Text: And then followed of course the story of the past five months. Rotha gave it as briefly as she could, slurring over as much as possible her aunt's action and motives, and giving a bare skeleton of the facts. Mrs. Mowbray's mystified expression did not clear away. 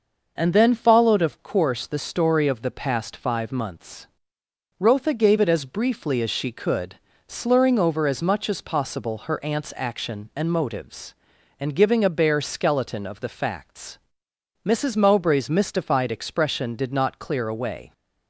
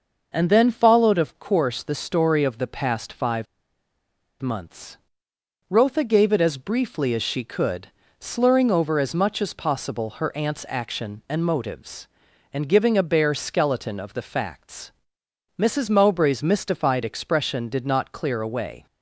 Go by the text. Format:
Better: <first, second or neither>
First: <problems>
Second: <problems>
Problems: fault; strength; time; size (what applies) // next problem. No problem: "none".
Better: first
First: none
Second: pauses between "five" and "months"; noticeable; at 3.4 s; 0.96 s long